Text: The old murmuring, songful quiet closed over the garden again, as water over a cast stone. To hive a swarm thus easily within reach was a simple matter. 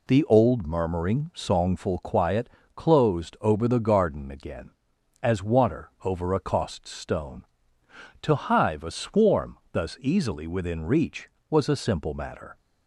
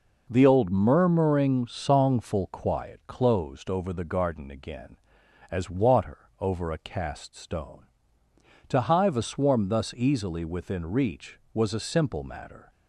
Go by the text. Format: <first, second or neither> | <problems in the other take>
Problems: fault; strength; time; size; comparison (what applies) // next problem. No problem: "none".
second | pauses between "quiet" and "closed"; slight; at 2.4 s; 0.28 s long // says "cost" for "cast"; at 6.3 s // pauses between "swarm" and "thus"; slight; at 9.5 s; 0.16 s long